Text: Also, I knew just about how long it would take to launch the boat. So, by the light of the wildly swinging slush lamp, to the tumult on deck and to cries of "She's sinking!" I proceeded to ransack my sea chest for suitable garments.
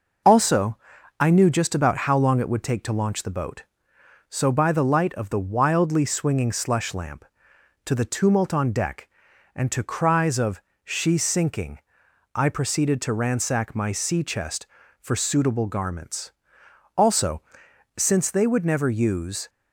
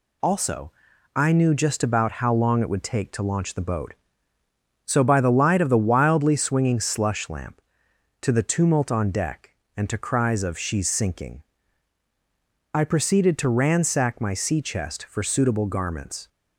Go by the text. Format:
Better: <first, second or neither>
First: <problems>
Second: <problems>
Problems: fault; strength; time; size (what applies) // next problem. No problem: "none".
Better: second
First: pauses between "of" and "She's"; slight; at 10.6 s; 0.24 s long // goes on to say "Also since they would never use"; strong; from 16.9 s on; 2.5 s long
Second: none